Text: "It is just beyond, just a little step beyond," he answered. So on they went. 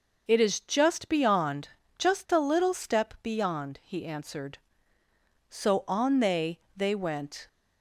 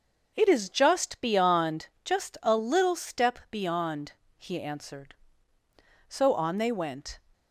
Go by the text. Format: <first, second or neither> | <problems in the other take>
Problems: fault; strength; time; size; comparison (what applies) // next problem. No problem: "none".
second | says "they" twice; at 6.7 s